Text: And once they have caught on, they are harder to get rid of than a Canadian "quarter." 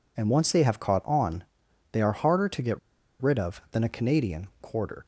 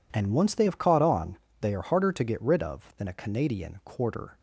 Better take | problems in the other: second | pauses between "get" and "rid"; at 2.7 s; 0.41 s long

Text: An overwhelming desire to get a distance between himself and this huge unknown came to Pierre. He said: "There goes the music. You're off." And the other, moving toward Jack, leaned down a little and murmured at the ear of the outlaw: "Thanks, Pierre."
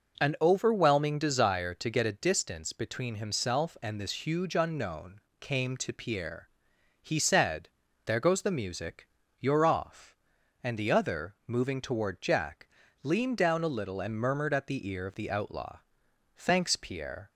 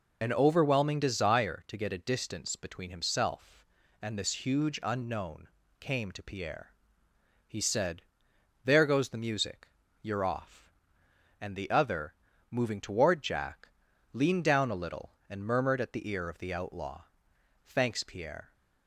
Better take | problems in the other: first | loses the start of "An"; at 0.2 s; 40 ms // pauses between "unknown" and "came"; slight; at 5.4 s; 0.32 s long; slight in the first

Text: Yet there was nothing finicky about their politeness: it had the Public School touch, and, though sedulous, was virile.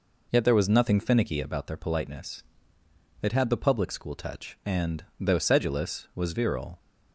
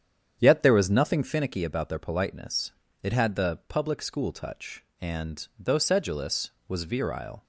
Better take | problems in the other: first | starts louder than the rest; strong; until 1.5 s; 8.5 dB

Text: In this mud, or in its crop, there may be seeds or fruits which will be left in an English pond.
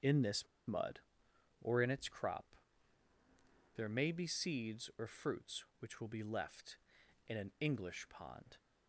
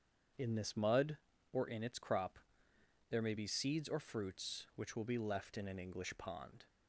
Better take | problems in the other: second | starts louder than the rest; strong; until 1.8 s; 7.5 dB; strong in the second // pauses between "this" and "mud"; slight; at 0.4 s; 0.20 s long

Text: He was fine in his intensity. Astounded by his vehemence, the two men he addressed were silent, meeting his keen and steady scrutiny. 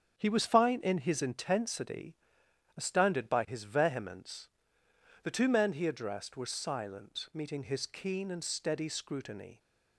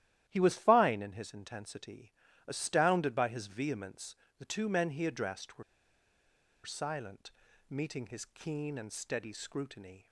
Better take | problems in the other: first | starts louder than the rest; strong; until 1.2 s; 12.5 dB; strong in the first // pauses between "were" and "silent"; at 5.6 s; 1.0 s long

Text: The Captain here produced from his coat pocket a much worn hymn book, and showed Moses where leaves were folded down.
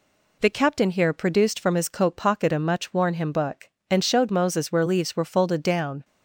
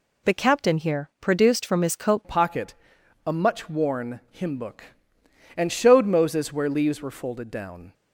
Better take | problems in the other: first | changes voice at "pocket"; from 2.2 s on; 5.7 s long // pauses between "pocket" and "a"; noticeable; at 2.7 s; 0.54 s long

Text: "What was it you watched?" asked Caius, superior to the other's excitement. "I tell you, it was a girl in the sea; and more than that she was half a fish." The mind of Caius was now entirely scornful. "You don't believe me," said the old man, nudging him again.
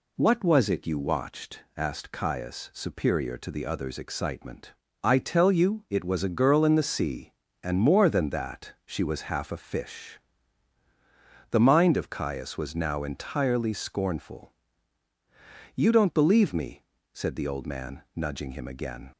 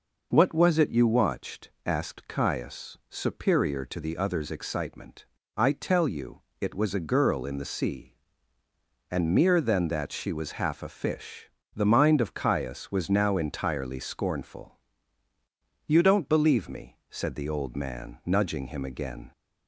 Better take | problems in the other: first | says "mere" for "more"; at 9.3 s

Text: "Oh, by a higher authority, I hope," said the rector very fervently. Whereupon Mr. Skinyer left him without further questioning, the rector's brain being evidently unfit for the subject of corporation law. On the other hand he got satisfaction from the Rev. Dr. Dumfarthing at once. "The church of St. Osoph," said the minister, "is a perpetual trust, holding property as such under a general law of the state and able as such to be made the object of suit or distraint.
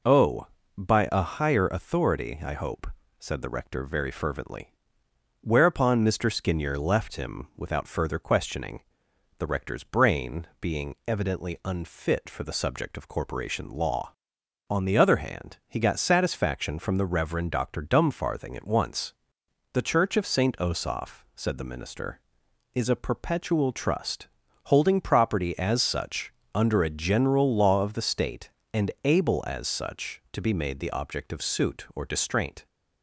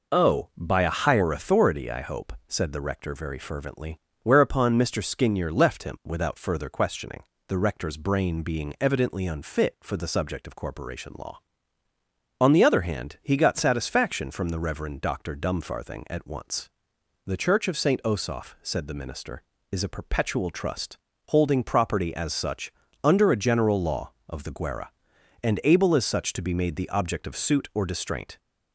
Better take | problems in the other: first | pauses between "such" and "under"; slight; at 22.7 s; 0.32 s long; slight in the first // says "guerra" for "state"; at 24.5 s

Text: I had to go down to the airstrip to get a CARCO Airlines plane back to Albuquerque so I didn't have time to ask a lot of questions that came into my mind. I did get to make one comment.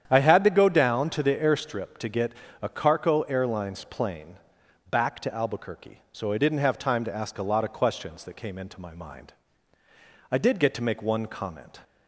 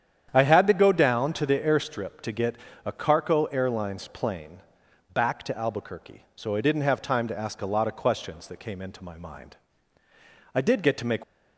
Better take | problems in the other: first | starts louder than the rest; strong; until 1.3 s; 9 dB; strong in the first // pauses between "get" and "a"; slight; at 2.5 s; 0.30 s long; slight in the first // pauses between "plane" and "back"; noticeable; at 4.5 s; 0.54 s long; noticeable in the first // stops before "one comment"; at 11.2 s

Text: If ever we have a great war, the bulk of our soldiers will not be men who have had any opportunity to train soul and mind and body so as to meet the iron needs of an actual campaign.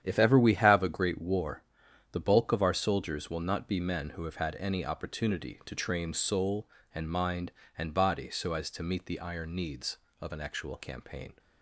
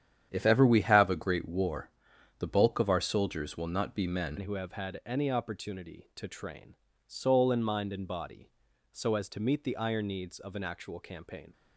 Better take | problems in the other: first | starts louder than the rest; strong; until 1.3 s; 9.5 dB; strong in the first // changes voice at "who"; from 4.3 s on; 7.2 s long // pauses between "train" and "soul"; slight; at 6.7 s; 0.32 s long

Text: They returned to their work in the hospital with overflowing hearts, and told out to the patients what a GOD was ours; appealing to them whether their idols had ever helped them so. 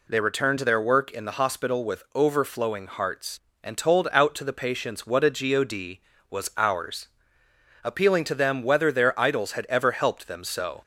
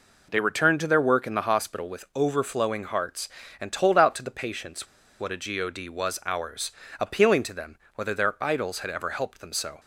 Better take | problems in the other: first | pauses between "patients" and "what"; slight; at 4.8 s; 0.34 s long // pauses between "them" and "whether"; slight; at 7.7 s; 0.18 s long

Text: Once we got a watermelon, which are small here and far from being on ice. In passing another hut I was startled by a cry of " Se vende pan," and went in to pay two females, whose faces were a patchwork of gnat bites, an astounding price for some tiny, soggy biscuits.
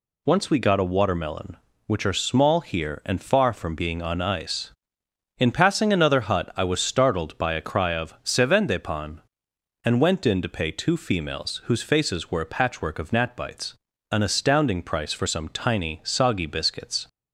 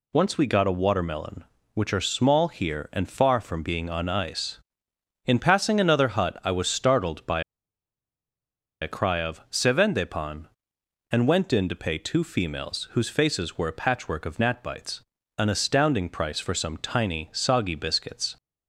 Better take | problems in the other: first | pauses between "by" and "a"; strong; at 7.4 s; 1.3 s long

